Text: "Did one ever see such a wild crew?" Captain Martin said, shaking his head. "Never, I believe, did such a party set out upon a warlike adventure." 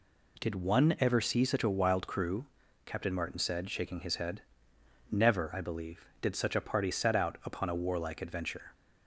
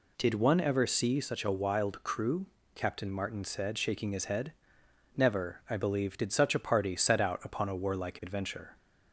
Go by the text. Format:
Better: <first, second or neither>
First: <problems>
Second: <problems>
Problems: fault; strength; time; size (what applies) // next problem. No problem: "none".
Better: neither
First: none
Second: none